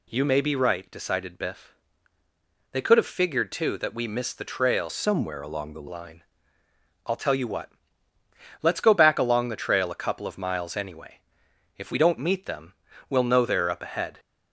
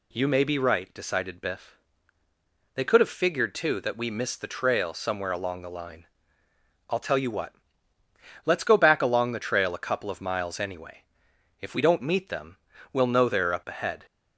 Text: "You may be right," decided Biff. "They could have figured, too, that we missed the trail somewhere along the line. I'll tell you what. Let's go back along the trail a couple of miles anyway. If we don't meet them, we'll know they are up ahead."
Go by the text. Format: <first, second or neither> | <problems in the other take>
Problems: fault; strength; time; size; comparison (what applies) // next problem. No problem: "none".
second | changes voice from "somewhere" to "the"; from 4.8 to 5.8 s; 1.0 s long